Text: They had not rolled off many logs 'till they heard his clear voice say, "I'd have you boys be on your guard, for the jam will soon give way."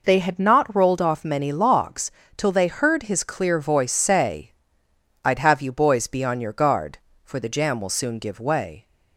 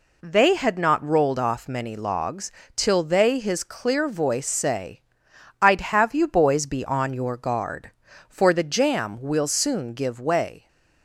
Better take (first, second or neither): first